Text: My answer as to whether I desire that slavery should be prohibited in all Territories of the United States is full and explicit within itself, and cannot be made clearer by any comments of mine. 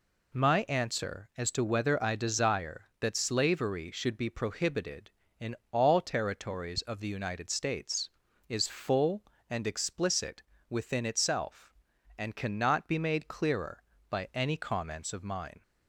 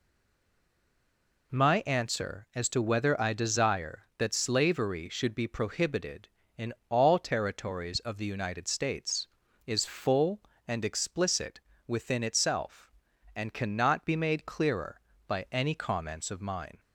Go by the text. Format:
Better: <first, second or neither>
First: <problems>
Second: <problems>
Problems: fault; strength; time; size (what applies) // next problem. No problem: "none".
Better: first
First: pauses between "in" and "all"; slight; at 5.5 s; 0.16 s long // pauses between "explicit" and "within"; slight; at 10.4 s; 0.26 s long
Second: stays silent before the first word; noticeable; until 1.5 s; 1.5 s long // pauses between "in" and "all"; slight; at 6.7 s; 0.16 s long // pauses between "explicit" and "within"; slight; at 11.6 s; 0.26 s long